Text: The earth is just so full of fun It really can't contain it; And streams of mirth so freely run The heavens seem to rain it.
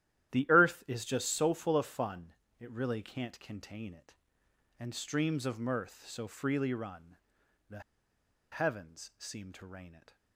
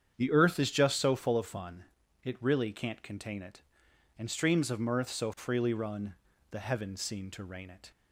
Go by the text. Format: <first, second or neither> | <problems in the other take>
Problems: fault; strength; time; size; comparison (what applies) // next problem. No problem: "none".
second | starts louder than the rest; strong; until 1.3 s; 12 dB; strong in the second // pauses between "fun" and "It"; slight; at 2.3 s; 0.28 s long; also in the second // pauses between "run" and "The"; noticeable; at 7.1 s; 0.52 s long; slight in the second // pauses between "The" and "heavens"; noticeable; at 7.8 s; 0.71 s long